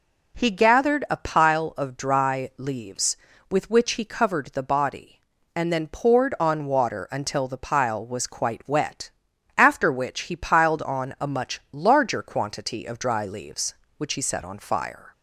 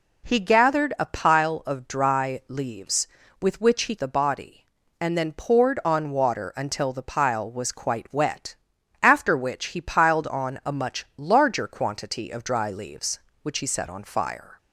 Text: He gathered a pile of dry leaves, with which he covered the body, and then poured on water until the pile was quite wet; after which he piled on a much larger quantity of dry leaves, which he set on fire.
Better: first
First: none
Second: skips "covered"; at 3.9 s

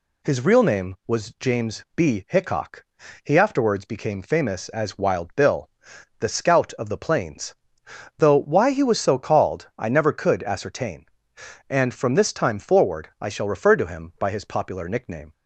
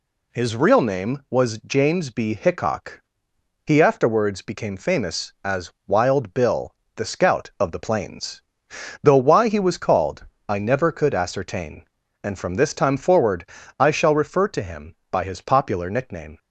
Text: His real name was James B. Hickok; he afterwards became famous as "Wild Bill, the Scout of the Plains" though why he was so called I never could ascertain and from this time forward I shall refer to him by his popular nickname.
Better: first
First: pauses between "Plains" and "though"; noticeable; at 7.5 s; 0.62 s long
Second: pauses between "as" and "Wild"; slight; at 5.7 s; 0.16 s long // pauses between "Plains" and "though"; noticeable; at 8.4 s; 0.62 s long // skips "so"; at 9.7 s // pauses between "called" and "I"; slight; at 10.2 s; 0.22 s long // pauses between "forward" and "I"; slight; at 13.4 s; 0.36 s long

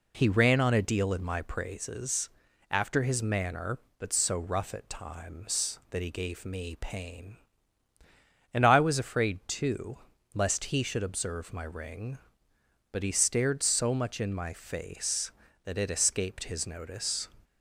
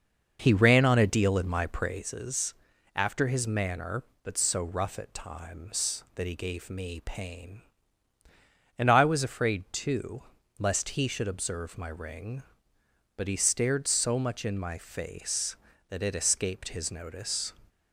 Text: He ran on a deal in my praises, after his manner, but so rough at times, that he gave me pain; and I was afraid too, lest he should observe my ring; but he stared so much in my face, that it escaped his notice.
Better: first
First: none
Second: starts louder than the rest; until 2.2 s; 6 dB

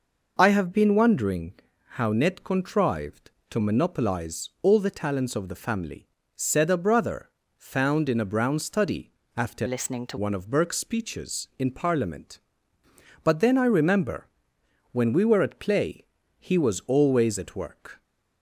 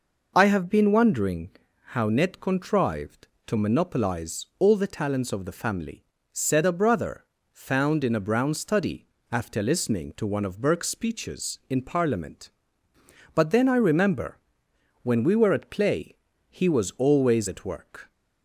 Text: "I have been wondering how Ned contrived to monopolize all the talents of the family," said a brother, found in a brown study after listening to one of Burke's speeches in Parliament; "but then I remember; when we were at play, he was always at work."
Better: second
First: pauses between "wondering" and "how"; at 1.5 s; 0.42 s long // pauses between "study" and "after"; slight; at 9.1 s; 0.20 s long // changes voice from "listening" to "to"; from 9.6 to 10.1 s; 0.5 s long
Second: pauses between "wondering" and "how"; at 1.5 s; 0.42 s long // pauses between "study" and "after"; slight; at 9.0 s; 0.20 s long

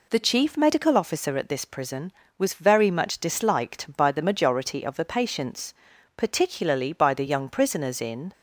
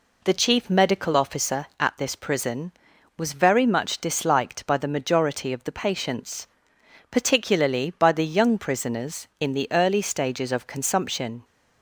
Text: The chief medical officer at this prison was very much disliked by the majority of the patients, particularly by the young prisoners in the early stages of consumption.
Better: second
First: stops before "the early stages of consumption"; at 8.3 s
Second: none

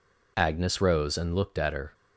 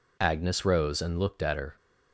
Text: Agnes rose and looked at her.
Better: neither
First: none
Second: none

